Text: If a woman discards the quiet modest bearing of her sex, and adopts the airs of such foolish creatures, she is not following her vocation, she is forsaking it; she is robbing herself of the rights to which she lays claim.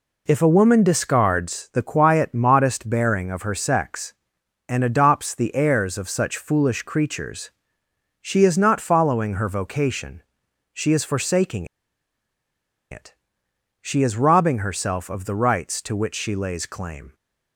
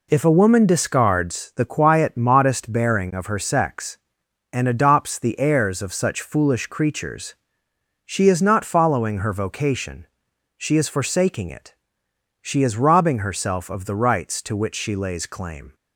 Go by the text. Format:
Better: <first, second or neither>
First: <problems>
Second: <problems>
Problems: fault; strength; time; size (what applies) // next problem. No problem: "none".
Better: second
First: pauses between "forsaking" and "it"; strong; at 11.6 s; 1.2 s long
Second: none